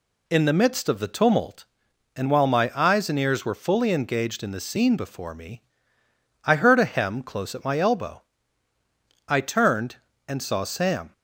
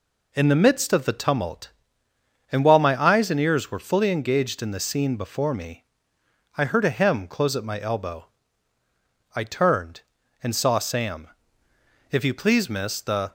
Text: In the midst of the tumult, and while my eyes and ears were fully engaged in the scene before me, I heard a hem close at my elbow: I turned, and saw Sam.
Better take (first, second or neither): first